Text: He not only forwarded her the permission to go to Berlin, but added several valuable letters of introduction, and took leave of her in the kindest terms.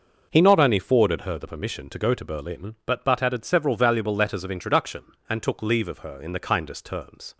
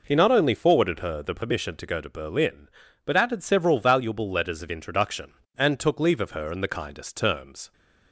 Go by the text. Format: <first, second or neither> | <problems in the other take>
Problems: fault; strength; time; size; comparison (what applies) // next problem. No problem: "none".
second | says "but" twice; at 3.0 s